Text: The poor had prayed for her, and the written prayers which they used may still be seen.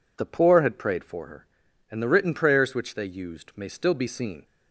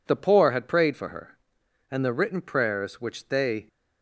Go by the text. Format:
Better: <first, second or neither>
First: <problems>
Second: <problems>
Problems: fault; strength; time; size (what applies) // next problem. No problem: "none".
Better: first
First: none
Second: stops before "used may still be seen"; at 3.6 s